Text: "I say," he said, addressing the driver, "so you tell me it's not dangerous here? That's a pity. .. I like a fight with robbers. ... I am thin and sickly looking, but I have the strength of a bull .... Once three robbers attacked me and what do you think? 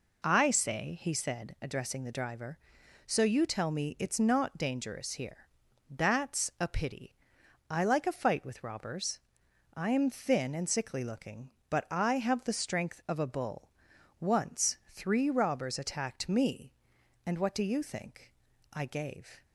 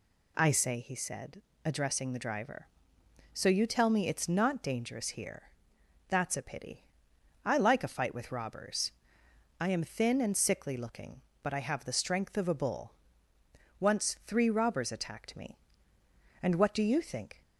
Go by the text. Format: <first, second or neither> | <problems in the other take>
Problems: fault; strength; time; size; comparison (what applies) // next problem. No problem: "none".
second | goes on to say "I gave"; noticeable; from 18.7 s on; 0.70 s long